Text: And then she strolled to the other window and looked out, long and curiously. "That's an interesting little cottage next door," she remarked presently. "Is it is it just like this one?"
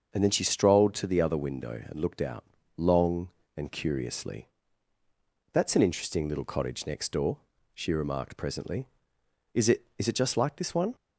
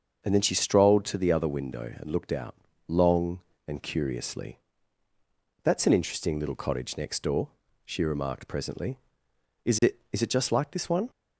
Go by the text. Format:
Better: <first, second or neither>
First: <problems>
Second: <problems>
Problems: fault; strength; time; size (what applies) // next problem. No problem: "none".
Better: neither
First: starts louder than the rest; until 1.1 s; 6.5 dB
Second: starts louder than the rest; until 1.2 s; 6.5 dB